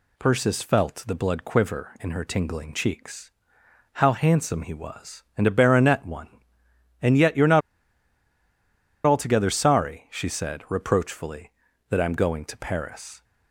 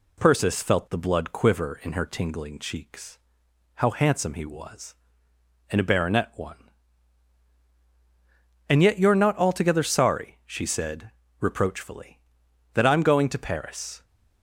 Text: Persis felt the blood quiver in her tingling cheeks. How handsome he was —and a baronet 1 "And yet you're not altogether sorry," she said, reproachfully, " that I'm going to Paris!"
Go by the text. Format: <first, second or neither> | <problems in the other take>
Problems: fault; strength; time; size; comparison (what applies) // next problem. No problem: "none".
second | pauses between "not" and "altogether"; strong; at 7.6 s; 1.4 s long